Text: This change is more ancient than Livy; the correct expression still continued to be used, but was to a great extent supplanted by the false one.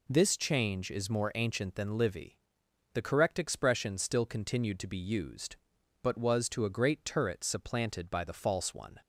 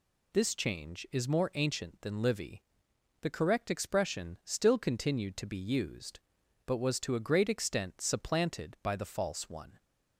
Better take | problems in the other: second | says "turret" for "extent"; at 7.0 s

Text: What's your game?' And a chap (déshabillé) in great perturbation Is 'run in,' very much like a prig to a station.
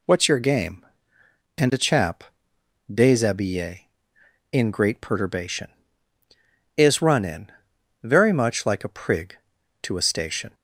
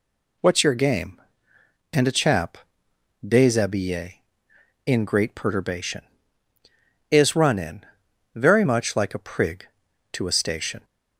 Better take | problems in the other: neither | none

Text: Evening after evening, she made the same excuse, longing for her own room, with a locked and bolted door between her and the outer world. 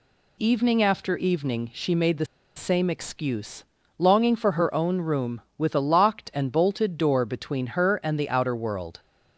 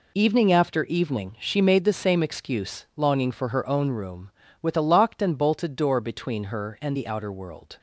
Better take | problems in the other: second | pauses between "the" and "same"; slight; at 2.2 s; 0.30 s long

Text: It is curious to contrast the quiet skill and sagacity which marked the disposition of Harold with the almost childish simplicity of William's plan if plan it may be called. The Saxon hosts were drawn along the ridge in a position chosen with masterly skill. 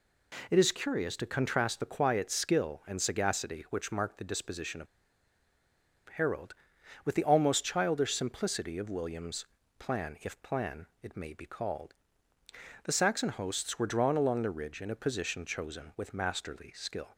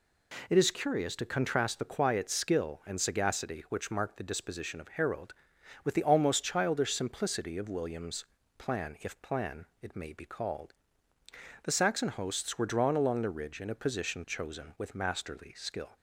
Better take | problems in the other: second | pauses between "of" and "Harold"; at 4.8 s; 1.2 s long // pauses between "William's" and "plan"; slight; at 9.4 s; 0.34 s long; slight in the second

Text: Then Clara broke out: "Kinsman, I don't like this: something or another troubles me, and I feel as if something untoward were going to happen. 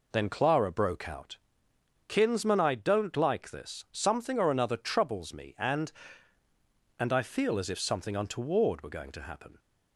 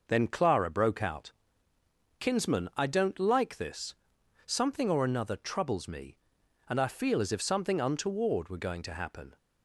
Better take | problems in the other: second | says "and" twice; at 6.9 s

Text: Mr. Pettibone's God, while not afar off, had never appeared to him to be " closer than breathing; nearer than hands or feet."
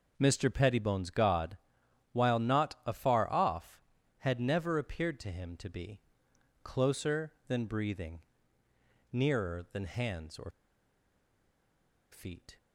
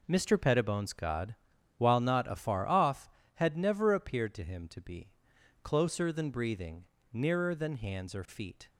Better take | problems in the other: second | pauses between "or" and "feet"; strong; at 10.5 s; 1.6 s long

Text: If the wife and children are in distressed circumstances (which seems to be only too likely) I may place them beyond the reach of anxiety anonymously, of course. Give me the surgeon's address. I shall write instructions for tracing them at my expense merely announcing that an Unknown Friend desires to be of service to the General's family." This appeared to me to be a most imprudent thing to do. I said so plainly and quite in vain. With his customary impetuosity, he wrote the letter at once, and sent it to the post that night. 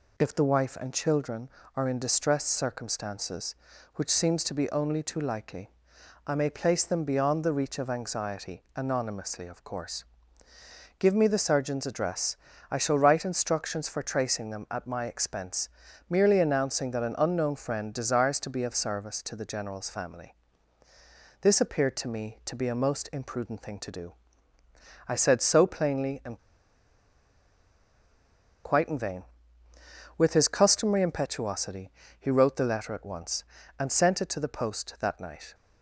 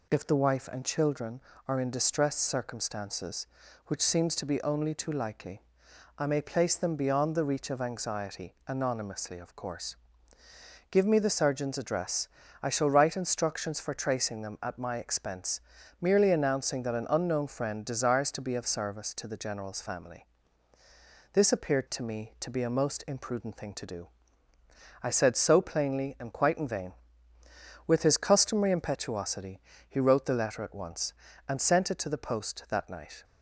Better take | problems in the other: second | pauses between "expense" and "merely"; at 15.6 s; 0.40 s long; also in the second // pauses between "and" and "quite"; strong; at 26.3 s; 2.2 s long

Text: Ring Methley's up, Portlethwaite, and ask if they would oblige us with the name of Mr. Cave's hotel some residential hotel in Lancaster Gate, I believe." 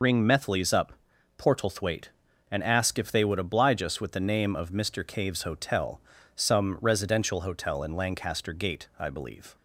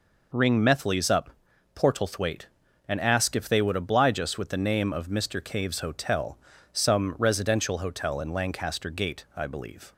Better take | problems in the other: second | loses the start of "Ring"; at 0.0 s; 65 ms // pauses between "hotel" and "some"; slight; at 6.0 s; 0.36 s long; slight in the second

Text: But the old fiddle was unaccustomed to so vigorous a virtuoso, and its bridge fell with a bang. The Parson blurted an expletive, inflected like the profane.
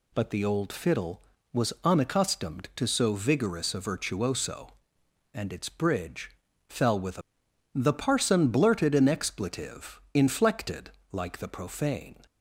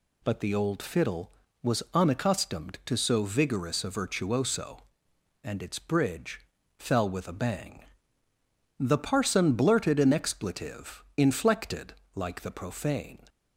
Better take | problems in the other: second | pauses between "bridge" and "fell"; at 6.3 s; 0.38 s long; also in the second // skips "bang"; at 7.4 s // pauses between "inflected" and "like"; slight; at 10.8 s; 0.22 s long; slight in the second

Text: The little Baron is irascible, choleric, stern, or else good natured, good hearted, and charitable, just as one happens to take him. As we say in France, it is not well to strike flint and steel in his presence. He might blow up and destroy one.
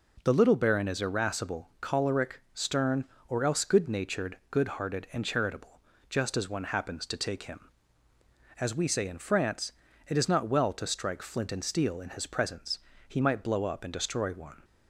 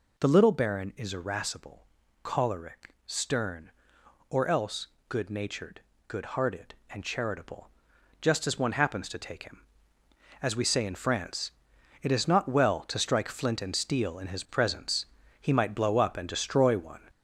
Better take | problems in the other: first | gets louder; noticeable; throughout; 5 dB // pauses between "else" and "good"; slight; at 4.8 s; 0.22 s long

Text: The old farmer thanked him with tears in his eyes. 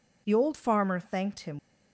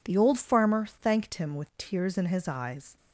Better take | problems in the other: second | stops before "with tears in his eyes"; at 1.5 s

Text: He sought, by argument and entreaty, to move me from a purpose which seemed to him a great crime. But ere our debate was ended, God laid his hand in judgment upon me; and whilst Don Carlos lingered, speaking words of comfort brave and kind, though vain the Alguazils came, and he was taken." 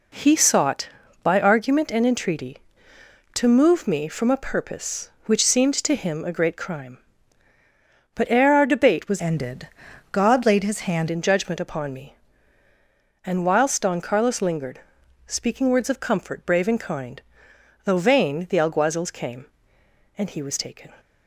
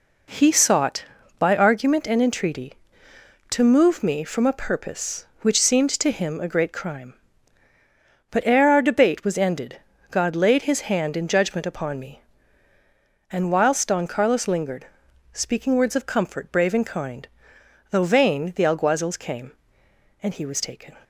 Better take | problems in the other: second | changes voice from "ended" to "hand"; from 9.1 to 11.0 s; 1.9 s long

